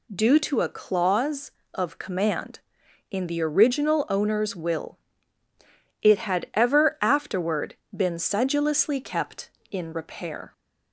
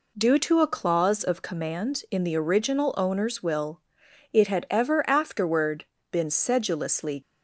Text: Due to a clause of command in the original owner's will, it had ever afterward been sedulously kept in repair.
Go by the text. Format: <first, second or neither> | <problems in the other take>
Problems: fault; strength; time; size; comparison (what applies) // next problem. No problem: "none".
first | pauses between "afterward" and "been"; slight; at 5.8 s; 0.26 s long; slight in the first // stops before "kept in repair"; at 7.2 s